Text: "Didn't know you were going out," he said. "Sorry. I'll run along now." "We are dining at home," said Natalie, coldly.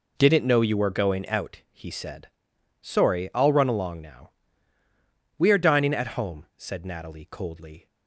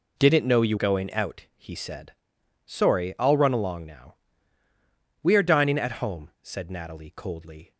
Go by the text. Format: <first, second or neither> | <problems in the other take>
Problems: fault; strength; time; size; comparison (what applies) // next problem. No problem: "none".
first | skips "were"; at 0.7 s